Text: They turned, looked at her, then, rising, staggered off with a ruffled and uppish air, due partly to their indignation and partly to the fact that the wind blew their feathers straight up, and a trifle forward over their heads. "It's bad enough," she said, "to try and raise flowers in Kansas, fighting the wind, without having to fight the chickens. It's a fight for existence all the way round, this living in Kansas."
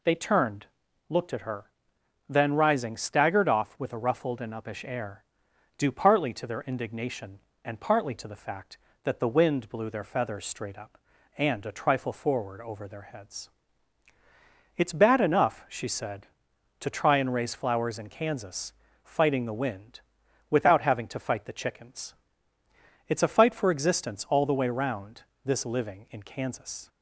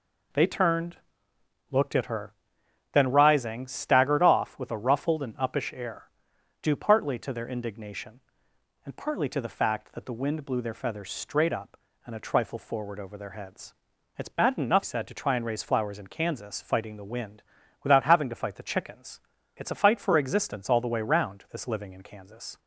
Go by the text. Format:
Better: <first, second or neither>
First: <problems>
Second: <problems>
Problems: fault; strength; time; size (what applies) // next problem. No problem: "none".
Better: first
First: none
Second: skips "she"; at 14.8 s